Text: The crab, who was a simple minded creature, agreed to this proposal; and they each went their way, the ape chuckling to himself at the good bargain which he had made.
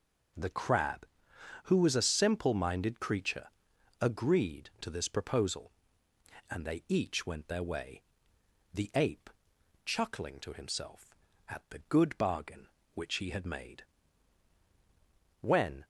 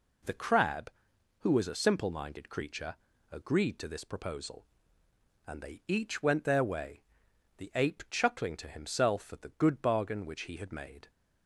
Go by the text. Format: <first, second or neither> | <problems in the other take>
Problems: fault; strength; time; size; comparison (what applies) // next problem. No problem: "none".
second | pauses between "ape" and "chuckling"; noticeable; at 9.2 s; 0.54 s long // goes on to say "When"; slight; from 15.4 s on; 0.42 s long